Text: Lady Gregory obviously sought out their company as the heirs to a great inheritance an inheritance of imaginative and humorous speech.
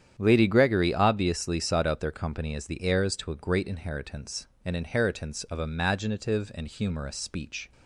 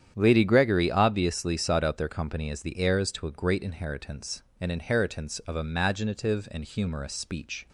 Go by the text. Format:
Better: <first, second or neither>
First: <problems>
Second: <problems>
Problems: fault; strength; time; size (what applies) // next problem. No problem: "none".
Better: neither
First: starts louder than the rest; strong; until 1.1 s; 9.5 dB // pauses between "inheritance" and "an"; slight; at 4.4 s; 0.18 s long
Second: starts louder than the rest; strong; until 1.1 s; 9.5 dB // pauses between "inheritance" and "an"; slight; at 4.4 s; 0.18 s long